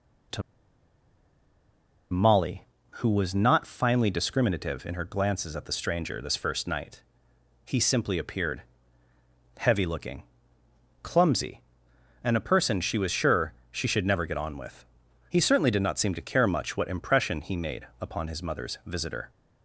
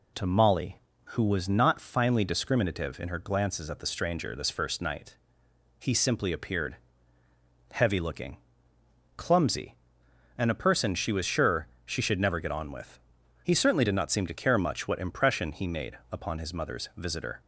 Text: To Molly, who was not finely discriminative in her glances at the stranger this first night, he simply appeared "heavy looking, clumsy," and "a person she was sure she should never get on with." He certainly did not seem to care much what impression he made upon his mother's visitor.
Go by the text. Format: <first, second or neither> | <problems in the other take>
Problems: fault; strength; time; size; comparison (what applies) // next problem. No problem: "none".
second | pauses between "To" and "Molly"; strong; at 0.4 s; 1.7 s long // pauses between "appeared" and "heavy"; noticeable; at 8.6 s; 0.96 s long; noticeable in the second // pauses between "sure" and "she"; slight; at 13.5 s; 0.18 s long; slight in the second